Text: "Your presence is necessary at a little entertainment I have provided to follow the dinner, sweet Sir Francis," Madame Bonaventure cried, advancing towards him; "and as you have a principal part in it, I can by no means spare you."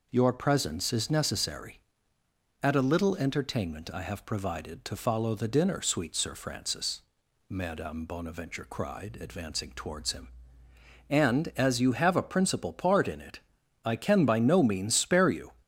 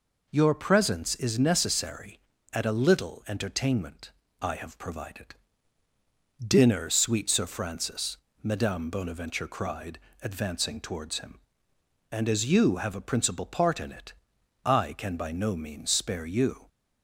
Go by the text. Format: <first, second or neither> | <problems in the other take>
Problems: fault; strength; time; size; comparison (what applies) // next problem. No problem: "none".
first | pauses between "entertainment" and "I"; slight; at 4.1 s; 0.30 s long // skips "to follow the"; at 5.8 s